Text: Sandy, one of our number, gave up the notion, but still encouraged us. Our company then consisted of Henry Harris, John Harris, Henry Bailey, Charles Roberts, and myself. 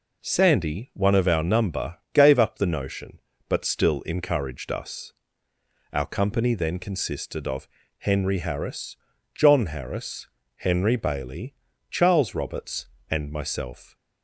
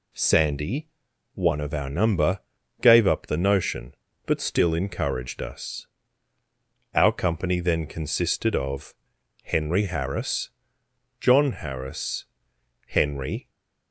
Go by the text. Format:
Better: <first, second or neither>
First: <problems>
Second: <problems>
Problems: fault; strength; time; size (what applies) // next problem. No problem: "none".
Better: first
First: pauses between "of" and "Henry"; slight; at 7.6 s; 0.30 s long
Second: pauses between "of" and "Henry"; noticeable; at 8.9 s; 0.50 s long // stays silent after the last word; slight; from 13.4 s on; 0.5 s long // stops before "Bailey Charles Roberts and myself"; at 13.4 s